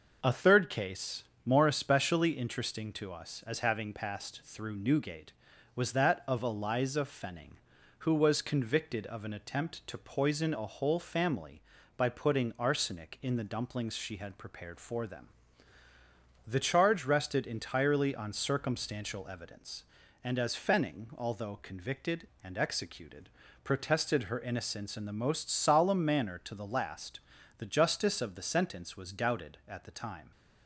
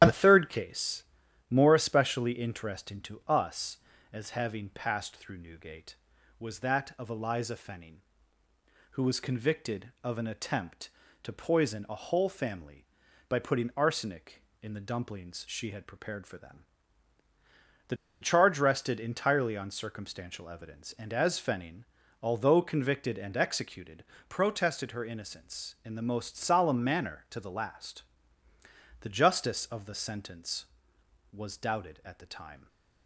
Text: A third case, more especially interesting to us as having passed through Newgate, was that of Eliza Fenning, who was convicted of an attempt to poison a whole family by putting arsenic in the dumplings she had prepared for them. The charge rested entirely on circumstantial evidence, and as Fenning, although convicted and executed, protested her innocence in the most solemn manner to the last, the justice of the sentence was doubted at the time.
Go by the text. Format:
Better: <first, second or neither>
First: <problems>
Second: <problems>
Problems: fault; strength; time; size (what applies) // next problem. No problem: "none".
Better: first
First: none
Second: starts louder than the rest; strong; until 1.0 s; 10.5 dB // pauses between "The" and "charge"; slight; at 17.9 s; 0.26 s long